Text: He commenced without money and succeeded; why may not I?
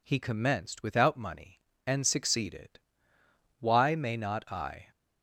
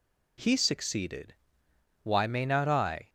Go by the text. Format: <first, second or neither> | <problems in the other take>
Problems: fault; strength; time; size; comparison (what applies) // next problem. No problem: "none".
first | skips "commenced without money and"; at 0.5 s